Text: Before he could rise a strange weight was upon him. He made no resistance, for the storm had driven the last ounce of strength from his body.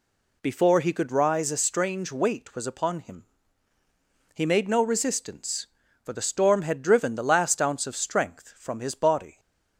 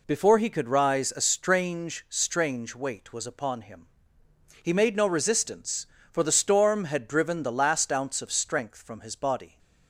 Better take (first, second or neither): first